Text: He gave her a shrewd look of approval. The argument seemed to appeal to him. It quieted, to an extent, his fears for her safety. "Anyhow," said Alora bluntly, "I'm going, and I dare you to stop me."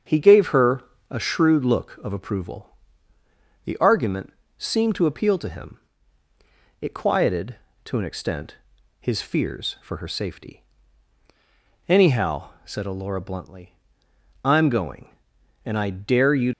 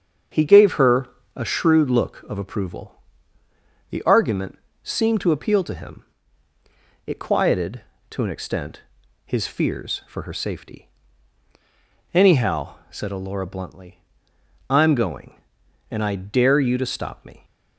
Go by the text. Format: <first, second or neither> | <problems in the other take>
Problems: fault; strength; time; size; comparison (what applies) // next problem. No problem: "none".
second | starts louder than the rest; until 1.3 s; 7 dB; also in the second // pauses between "her" and "a"; slight; at 0.8 s; 0.28 s long; slight in the second // pauses between "argument" and "seemed"; slight; at 4.3 s; 0.26 s long; slight in the second // stops before "to stop me"; at 16.5 s